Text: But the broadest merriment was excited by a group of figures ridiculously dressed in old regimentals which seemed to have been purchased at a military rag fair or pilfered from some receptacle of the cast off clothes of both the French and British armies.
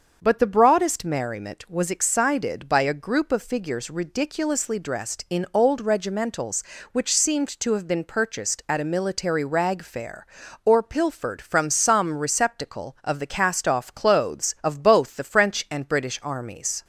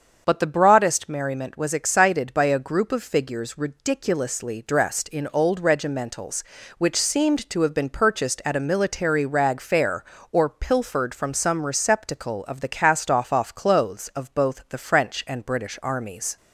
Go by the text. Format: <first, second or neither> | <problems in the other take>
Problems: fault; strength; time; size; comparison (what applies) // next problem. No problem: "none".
first | starts louder than the rest; until 1.2 s; 7 dB; also in the first // says "off" twice; at 13.3 s